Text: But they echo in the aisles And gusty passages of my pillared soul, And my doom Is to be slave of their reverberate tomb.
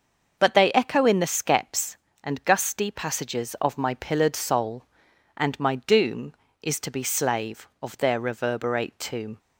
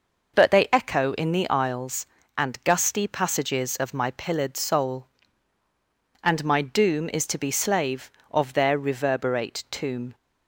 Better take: second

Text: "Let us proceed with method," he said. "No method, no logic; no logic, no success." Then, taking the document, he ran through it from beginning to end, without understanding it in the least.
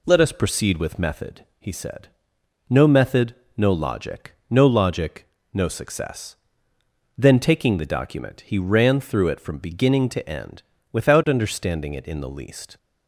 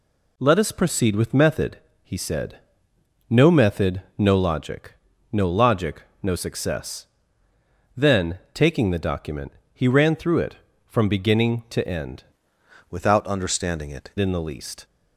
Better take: first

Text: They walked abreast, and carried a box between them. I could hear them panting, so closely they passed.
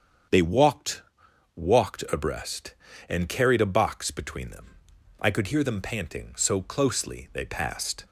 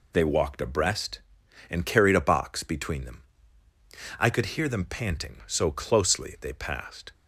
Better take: second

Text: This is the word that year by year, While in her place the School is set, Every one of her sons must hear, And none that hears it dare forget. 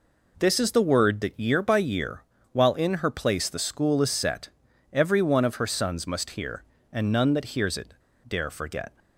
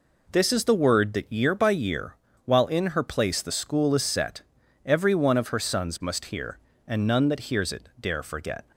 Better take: second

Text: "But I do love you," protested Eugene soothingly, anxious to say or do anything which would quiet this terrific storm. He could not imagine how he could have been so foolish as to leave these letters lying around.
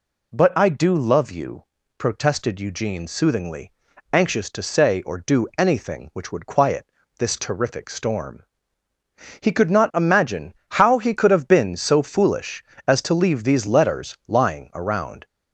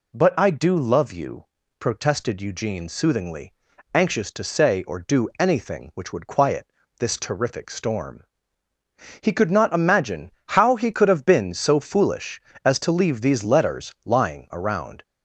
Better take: neither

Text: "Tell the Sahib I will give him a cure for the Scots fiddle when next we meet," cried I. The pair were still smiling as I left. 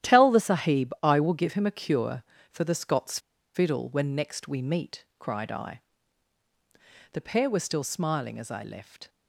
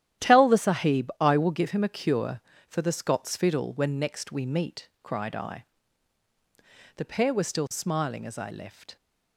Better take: second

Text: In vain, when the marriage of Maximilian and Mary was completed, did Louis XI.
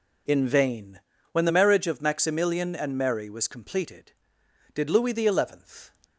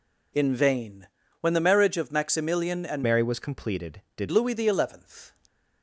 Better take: first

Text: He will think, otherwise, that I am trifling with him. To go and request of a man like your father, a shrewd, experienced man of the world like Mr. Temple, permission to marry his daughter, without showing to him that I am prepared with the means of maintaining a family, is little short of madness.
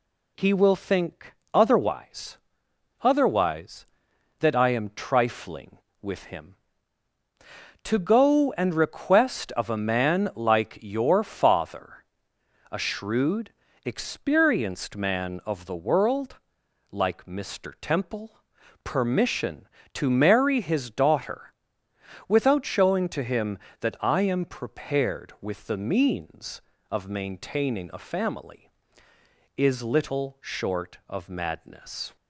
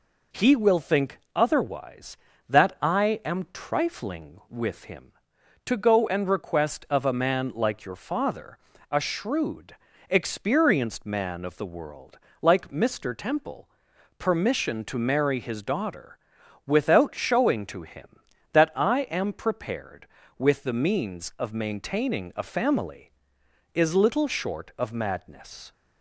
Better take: second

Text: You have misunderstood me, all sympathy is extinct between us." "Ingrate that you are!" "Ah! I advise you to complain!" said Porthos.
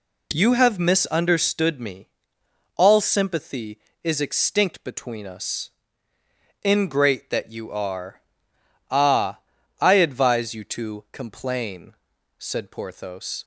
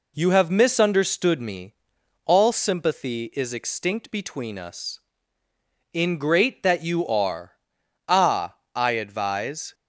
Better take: first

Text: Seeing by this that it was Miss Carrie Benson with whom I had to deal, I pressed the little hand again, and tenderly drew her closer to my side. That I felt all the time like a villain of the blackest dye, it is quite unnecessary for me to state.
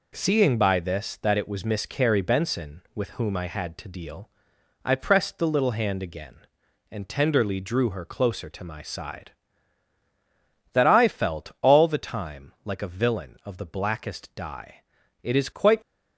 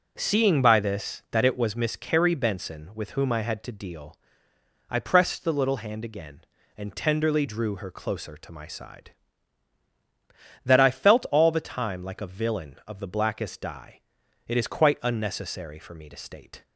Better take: second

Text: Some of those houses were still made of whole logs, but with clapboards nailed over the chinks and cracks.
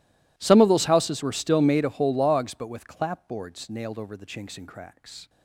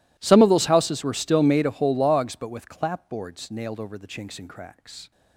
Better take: neither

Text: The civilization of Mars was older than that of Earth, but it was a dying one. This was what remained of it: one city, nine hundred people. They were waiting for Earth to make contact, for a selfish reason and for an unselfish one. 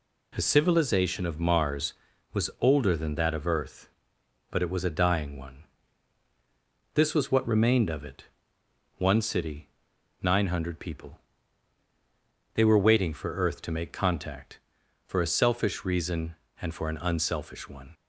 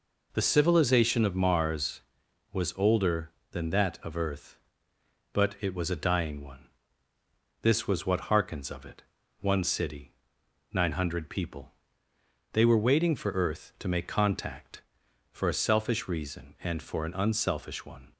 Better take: first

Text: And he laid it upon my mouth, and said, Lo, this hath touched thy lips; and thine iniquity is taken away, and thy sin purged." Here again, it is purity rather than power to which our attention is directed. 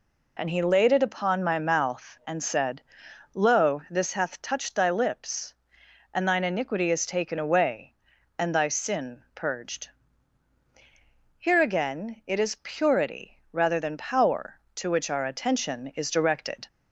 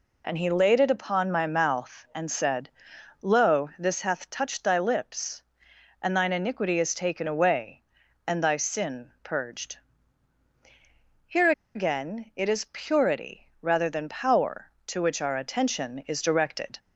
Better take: first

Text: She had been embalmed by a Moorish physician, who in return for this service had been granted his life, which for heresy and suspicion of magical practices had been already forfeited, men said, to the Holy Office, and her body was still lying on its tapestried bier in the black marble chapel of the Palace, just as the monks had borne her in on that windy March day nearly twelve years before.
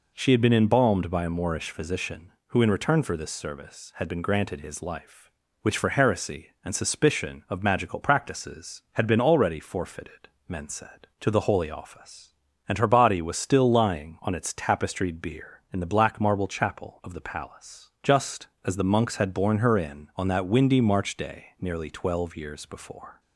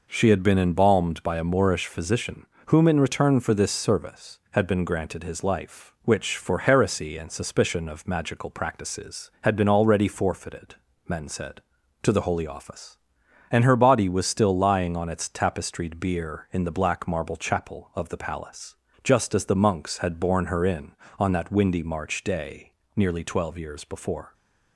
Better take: first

